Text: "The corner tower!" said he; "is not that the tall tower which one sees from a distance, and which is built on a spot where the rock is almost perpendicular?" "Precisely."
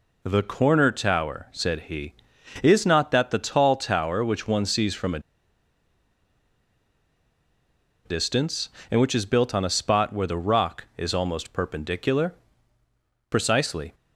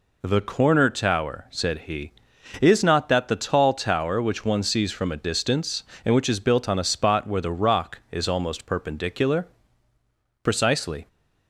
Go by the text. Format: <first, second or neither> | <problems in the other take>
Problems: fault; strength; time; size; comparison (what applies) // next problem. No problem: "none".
second | pauses between "a" and "distance"; strong; at 5.1 s; 2.8 s long